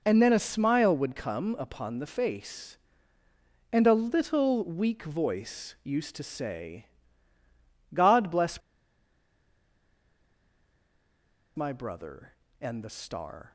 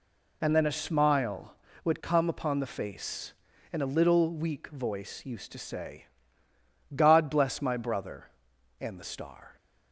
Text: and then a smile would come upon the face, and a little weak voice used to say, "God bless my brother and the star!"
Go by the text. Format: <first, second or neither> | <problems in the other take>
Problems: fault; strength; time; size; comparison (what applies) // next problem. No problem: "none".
second | pauses between "bless" and "my"; strong; at 8.6 s; 2.9 s long